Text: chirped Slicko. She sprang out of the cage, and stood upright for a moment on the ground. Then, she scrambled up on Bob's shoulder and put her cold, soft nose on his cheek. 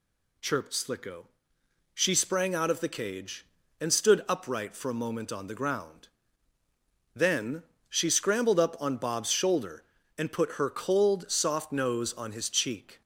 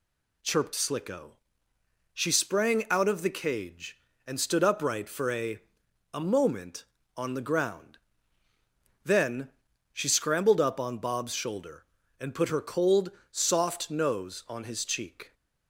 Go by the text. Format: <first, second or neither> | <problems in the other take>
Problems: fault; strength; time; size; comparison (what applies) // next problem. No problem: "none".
first | says "a" twice; at 6.1 s